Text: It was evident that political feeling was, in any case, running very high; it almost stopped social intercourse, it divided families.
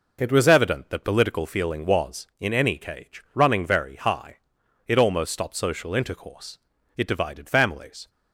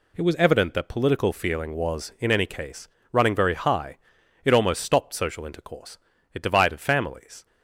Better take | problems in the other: second | says "cage" for "case"; at 2.7 s

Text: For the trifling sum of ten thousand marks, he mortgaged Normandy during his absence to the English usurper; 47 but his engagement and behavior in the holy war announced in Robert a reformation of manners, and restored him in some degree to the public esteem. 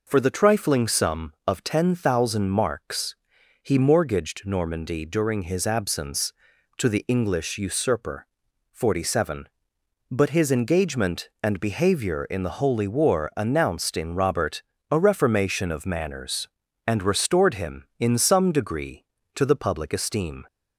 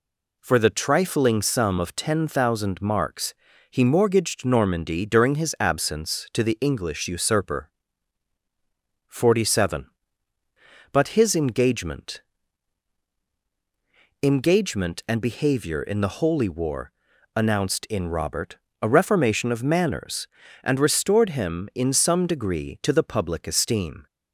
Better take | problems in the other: first | says "engagement" twice; at 14.2 s // pauses between "war" and "announced"; at 16.9 s; 0.44 s long // pauses between "Robert" and "a"; slight; at 18.5 s; 0.24 s long; slight in the first

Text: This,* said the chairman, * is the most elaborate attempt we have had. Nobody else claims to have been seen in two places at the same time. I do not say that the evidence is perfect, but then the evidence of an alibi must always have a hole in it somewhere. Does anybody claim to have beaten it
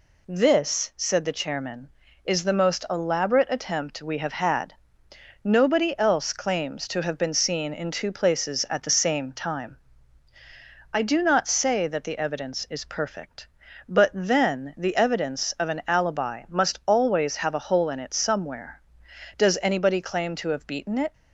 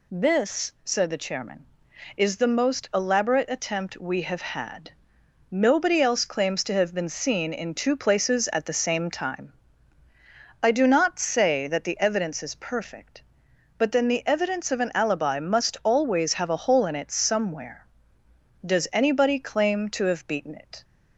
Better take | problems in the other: neither | none

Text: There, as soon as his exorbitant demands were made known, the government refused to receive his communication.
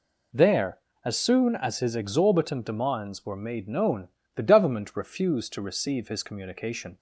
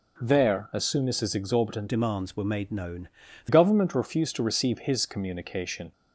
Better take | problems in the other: first | changes voice from "demands" to "the"; from 1.8 to 3.4 s; 1.6 s long

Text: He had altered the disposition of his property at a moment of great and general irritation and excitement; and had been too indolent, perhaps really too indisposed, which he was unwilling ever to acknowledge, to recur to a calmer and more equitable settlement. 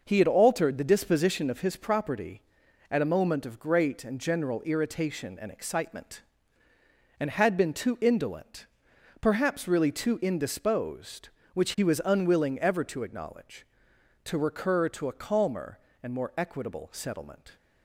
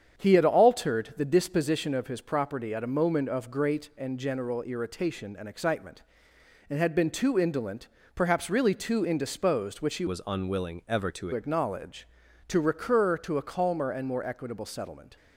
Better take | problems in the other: first | starts louder than the rest; strong; until 1.2 s; 8 dB // changes voice from "was" to "to"; from 10.0 to 11.2 s; 1.2 s long

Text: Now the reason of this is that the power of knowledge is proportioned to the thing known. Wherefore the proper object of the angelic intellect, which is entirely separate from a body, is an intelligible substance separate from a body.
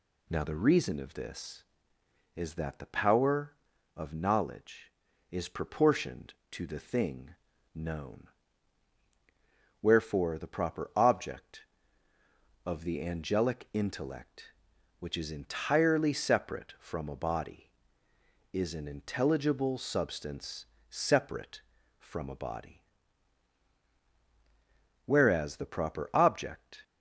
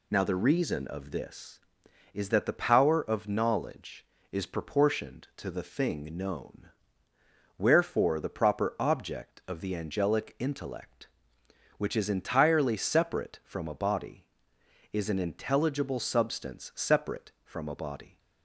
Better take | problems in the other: second | pauses between "thing" and "known"; at 7.3 s; 0.38 s long // pauses between "substance" and "separate"; slight; at 20.6 s; 0.24 s long // goes on to say "Whereas the proper object"; strong; from 25.0 s on; 1.7 s long

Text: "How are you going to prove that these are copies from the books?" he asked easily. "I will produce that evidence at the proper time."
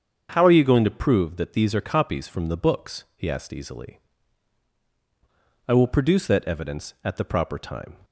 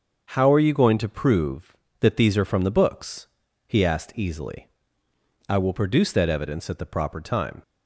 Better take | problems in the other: first | starts louder than the rest; until 1.2 s; 6.5 dB; strong in the first // skips "copies"; at 2.4 s

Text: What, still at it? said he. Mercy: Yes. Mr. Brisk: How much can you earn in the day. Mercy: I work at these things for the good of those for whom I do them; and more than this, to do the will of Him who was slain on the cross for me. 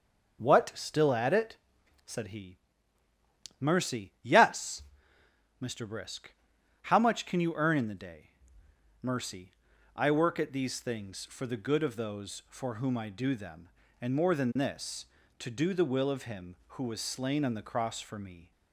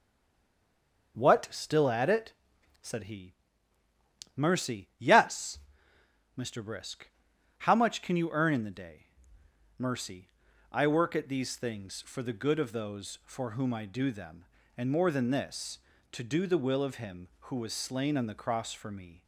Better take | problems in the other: first | stays silent before the first word; until 1.1 s; 1.1 s long // starts louder than the rest; until 2.1 s; 6 dB; also in the first

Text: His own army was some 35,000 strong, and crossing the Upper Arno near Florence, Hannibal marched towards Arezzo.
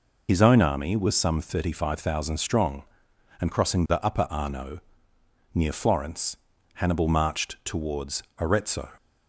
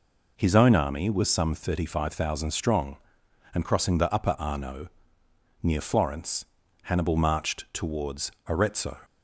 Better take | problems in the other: second | loses the start of "His"; at 0.2 s; 50 ms // pauses between "Arno" and "near"; noticeable; at 4.7 s; 0.74 s long; noticeable in the second // pauses between "towards" and "Arezzo"; slight; at 8.2 s; 0.16 s long; slight in the second

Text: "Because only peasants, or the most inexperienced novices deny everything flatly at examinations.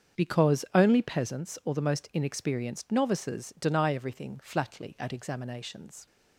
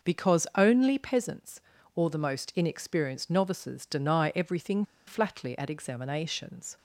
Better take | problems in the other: first | starts louder than the rest; until 1.1 s; 6 dB; strong in the first // pauses between "everything" and "flatly"; slight; at 4.8 s; 0.23 s long

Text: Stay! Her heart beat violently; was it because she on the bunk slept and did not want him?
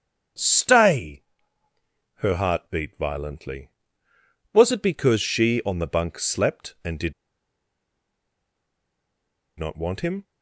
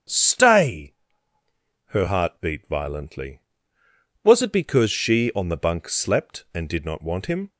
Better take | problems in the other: second | starts louder than the rest; strong; until 2.3 s; 8 dB; strong in the second // pauses between "did" and "not"; strong; at 7.1 s; 2.4 s long

